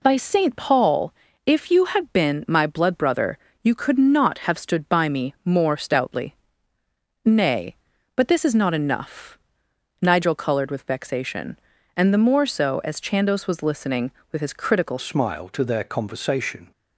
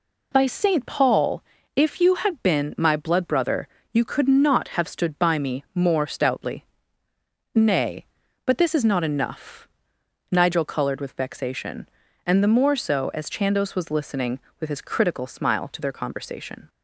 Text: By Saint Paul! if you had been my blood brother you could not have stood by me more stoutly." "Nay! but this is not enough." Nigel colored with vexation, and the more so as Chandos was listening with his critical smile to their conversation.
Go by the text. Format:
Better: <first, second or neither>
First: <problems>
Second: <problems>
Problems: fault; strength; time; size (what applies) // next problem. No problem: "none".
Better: second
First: pauses between "brother" and "you"; slight; at 3.3 s; 0.26 s long // changes voice at "smile"; from 14.9 s on; 1.8 s long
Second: pauses between "brother" and "you"; slight; at 3.6 s; 0.26 s long